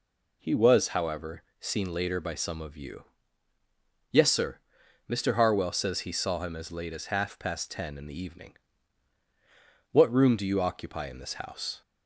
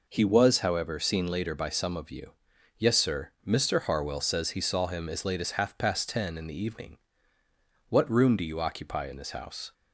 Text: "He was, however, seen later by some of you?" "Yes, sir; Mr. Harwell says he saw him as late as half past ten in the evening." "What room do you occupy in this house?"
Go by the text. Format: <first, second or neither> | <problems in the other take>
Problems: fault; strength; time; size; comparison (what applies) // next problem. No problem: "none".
neither | none